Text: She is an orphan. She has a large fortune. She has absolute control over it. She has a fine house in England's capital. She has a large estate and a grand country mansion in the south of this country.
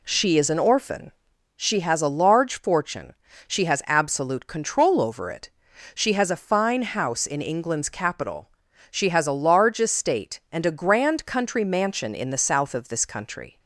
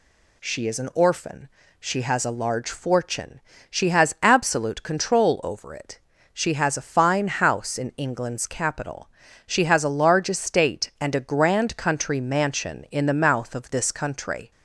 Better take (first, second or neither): first